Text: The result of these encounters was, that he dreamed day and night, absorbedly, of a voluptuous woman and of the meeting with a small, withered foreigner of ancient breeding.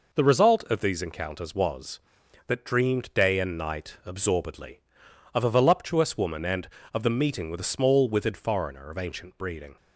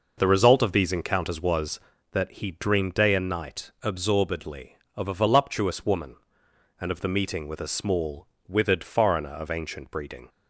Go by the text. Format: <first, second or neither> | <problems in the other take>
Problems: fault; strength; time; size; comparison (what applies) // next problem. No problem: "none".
second | skips "he"; at 2.6 s